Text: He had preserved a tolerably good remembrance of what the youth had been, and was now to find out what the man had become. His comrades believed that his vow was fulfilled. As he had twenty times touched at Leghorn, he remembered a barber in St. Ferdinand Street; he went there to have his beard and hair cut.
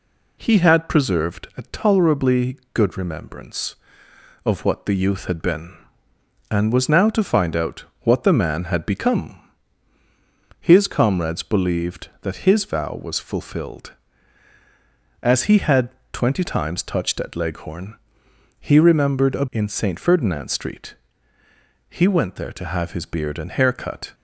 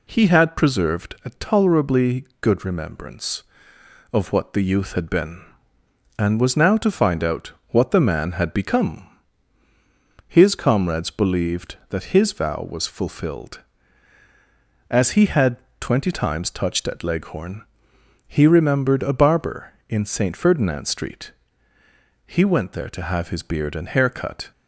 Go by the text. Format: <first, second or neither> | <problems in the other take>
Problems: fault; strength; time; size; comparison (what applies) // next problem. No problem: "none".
second | pauses between "out" and "what"; slight; at 7.8 s; 0.20 s long; slight in the second // pauses between "had" and "twenty"; slight; at 15.8 s; 0.24 s long; slight in the second // skips "barber"; at 19.4 s